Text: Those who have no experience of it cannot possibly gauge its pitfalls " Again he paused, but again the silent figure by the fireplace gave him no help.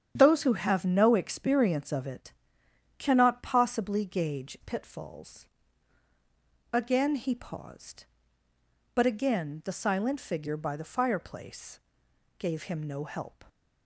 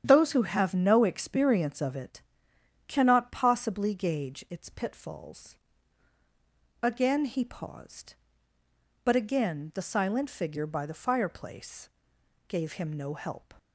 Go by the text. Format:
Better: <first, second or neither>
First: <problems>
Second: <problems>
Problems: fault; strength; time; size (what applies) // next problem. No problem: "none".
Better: second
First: starts louder than the rest; strong; until 1.1 s; 9.5 dB // pauses between "it" and "cannot"; noticeable; at 2.3 s; 0.64 s long // skips "its"; at 4.5 s // pauses between "fireplace" and "gave"; noticeable; at 11.7 s; 0.62 s long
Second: starts louder than the rest; strong; until 1.0 s; 9.5 dB // pauses between "it" and "cannot"; noticeable; at 2.2 s; 0.64 s long // pauses between "fireplace" and "gave"; noticeable; at 11.8 s; 0.62 s long